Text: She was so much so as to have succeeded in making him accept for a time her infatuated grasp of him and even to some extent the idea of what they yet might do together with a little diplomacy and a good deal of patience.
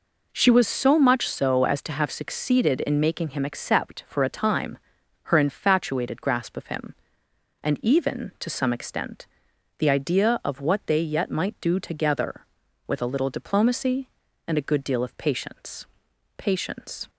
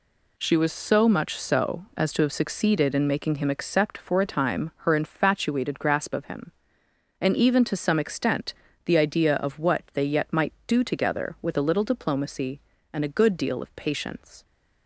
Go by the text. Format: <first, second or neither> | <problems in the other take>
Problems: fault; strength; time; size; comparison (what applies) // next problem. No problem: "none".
second | pauses between "time" and "her"; noticeable; at 4.7 s; 0.46 s long // pauses between "extent" and "the"; noticeable; at 9.2 s; 0.54 s long; slight in the second // says "patience" twice; at 16.3 s